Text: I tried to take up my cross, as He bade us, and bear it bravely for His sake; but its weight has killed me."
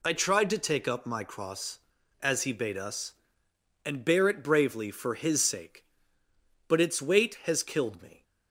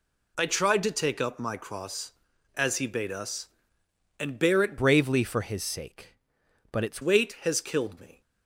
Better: first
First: none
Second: changes voice from "bravely" to "its"; from 4.7 to 7.0 s; 2.3 s long

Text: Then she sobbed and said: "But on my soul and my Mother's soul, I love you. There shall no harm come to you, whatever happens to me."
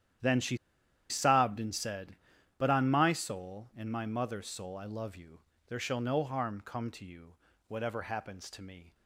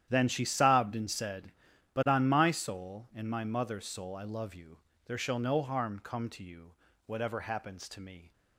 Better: second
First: starts louder than the rest; strong; until 1.7 s; 10.5 dB // pauses between "she" and "sobbed"; noticeable; at 0.5 s; 0.53 s long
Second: starts louder than the rest; strong; until 1.1 s; 10.5 dB

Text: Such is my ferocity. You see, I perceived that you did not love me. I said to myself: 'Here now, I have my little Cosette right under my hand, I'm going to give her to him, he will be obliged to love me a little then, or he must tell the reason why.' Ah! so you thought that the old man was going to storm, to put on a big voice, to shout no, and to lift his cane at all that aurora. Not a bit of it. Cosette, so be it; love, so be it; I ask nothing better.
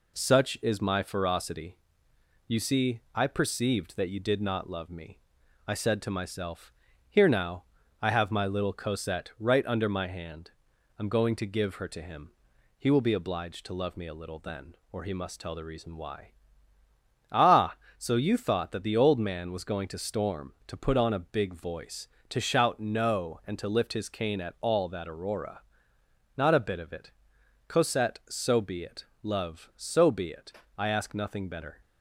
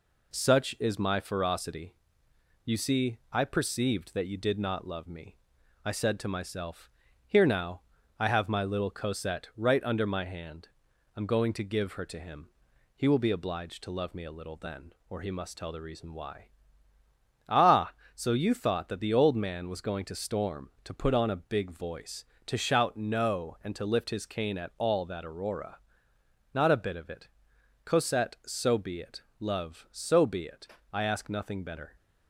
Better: neither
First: none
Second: none

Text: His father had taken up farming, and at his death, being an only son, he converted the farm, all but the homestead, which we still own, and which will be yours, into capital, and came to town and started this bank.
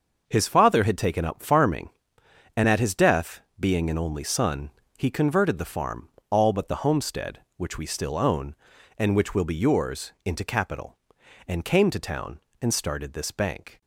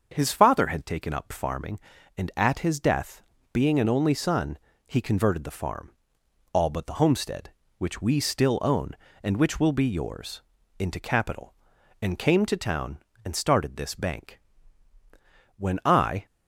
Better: first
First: starts louder than the rest; until 1.2 s; 6 dB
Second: starts louder than the rest; until 1.1 s; 6.5 dB // goes on to say "When I"; noticeable; from 15.5 s on; 0.68 s long

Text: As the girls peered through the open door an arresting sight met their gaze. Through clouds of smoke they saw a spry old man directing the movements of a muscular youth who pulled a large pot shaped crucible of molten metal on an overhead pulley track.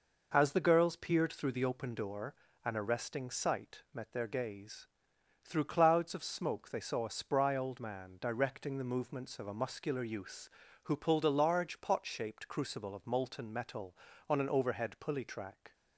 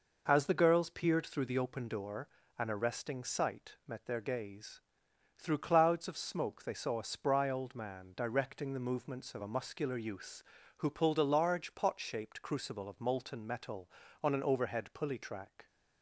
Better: neither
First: pauses between "door" and "an"; slight; at 2.3 s; 0.32 s long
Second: pauses between "door" and "an"; slight; at 2.2 s; 0.32 s long

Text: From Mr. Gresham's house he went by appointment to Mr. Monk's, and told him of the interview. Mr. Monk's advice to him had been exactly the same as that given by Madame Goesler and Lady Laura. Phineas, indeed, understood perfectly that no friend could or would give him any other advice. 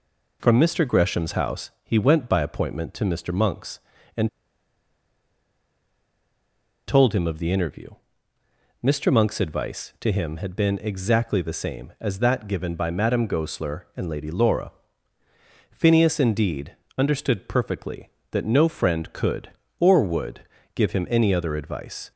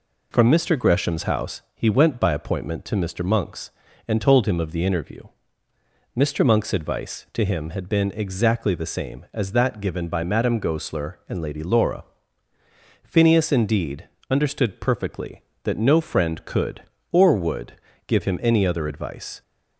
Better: second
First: pauses between "and" and "told"; strong; at 4.2 s; 2.6 s long // pauses between "would" and "give"; slight; at 20.4 s; 0.34 s long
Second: pauses between "would" and "give"; slight; at 17.7 s; 0.34 s long

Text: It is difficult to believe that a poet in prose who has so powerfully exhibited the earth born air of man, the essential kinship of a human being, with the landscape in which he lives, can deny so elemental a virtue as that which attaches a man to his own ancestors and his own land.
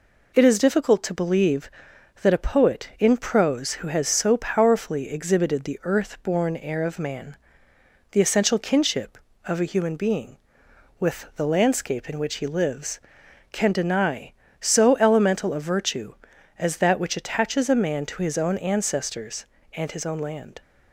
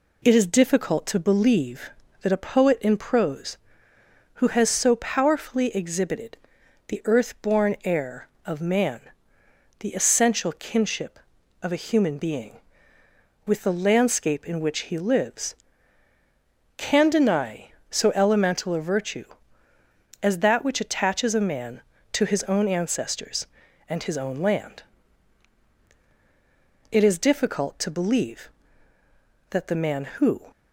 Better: first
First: none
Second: pauses between "exhibited" and "the"; noticeable; at 6.3 s; 0.52 s long // goes on to say "It is difficult to believe that the man who"; strong; from 26.9 s on; 3.5 s long

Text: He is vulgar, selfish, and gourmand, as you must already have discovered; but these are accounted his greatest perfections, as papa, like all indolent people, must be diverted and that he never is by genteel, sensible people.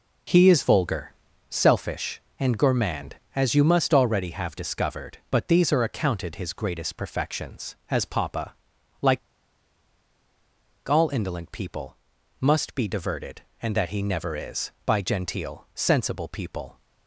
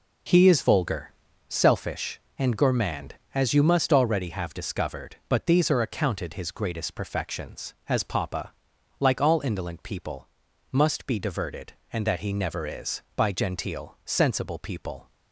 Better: second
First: pauses between "like" and "all"; strong; at 9.1 s; 1.6 s long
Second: none

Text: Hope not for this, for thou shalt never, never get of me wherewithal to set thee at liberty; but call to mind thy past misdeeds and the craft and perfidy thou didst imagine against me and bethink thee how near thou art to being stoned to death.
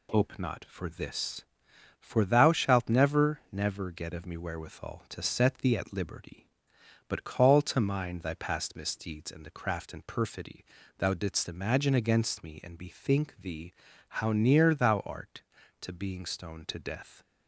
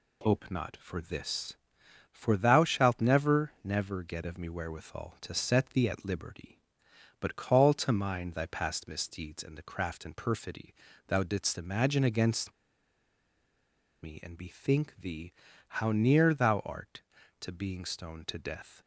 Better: first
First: pauses between "perfidy" and "thou"; slight; at 10.6 s; 0.32 s long // pauses between "thee" and "how"; noticeable; at 13.7 s; 0.48 s long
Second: pauses between "perfidy" and "thou"; slight; at 10.7 s; 0.32 s long // pauses between "against" and "me"; strong; at 12.5 s; 1.5 s long // pauses between "thee" and "how"; noticeable; at 15.3 s; 0.48 s long

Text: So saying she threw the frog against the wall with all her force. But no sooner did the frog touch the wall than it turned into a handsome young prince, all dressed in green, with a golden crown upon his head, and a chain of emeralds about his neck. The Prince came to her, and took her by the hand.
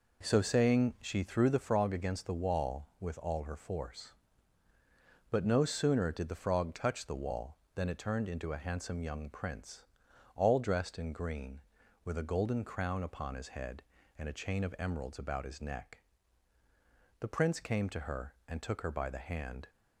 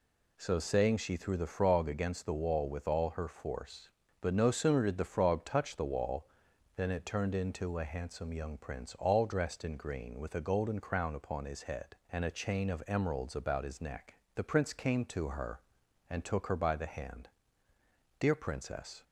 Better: first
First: none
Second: goes on to say "Dear Princess"; noticeable; from 18.1 s on; 0.86 s long

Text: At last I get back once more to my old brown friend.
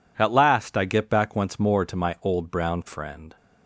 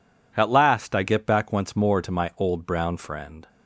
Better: neither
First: none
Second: none

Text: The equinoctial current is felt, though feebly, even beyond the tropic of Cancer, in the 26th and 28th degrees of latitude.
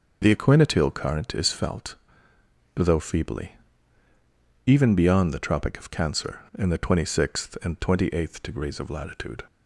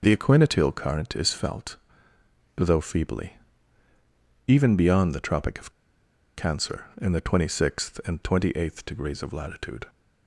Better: first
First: none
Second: pauses between "of" and "Cancer"; noticeable; at 5.7 s; 0.64 s long

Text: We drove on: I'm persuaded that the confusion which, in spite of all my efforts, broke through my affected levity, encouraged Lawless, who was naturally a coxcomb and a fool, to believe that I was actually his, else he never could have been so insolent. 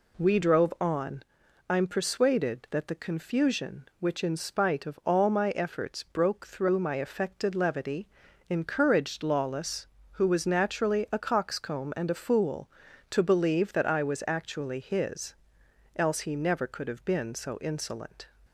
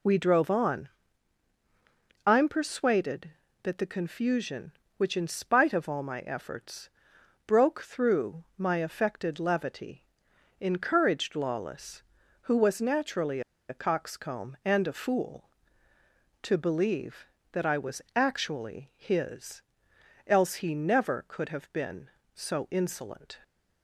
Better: first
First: none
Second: pauses between "naturally" and "a"; slight; at 13.4 s; 0.28 s long

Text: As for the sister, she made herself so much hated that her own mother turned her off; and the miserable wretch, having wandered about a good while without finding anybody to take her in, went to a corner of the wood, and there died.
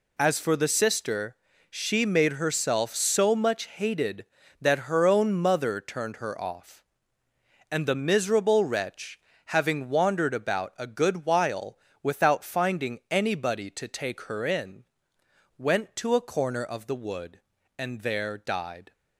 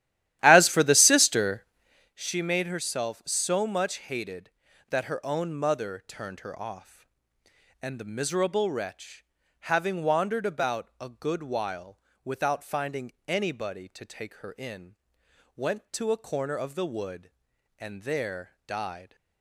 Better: first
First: pauses between "while" and "without"; slight; at 11.7 s; 0.24 s long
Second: starts louder than the rest; strong; until 2.2 s; 13 dB // pauses between "while" and "without"; slight; at 11.9 s; 0.24 s long // pauses between "finding" and "anybody"; slight; at 13.1 s; 0.16 s long

